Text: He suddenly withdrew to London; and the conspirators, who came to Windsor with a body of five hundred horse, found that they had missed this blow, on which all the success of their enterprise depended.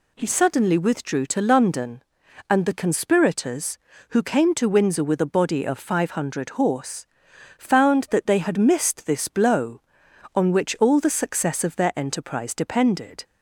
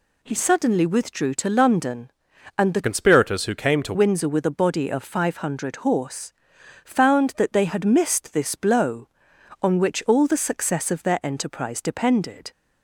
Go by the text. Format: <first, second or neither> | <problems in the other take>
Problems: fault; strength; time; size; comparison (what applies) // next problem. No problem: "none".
first | changes voice from "conspirators" to "to"; from 2.8 to 3.9 s; 1.1 s long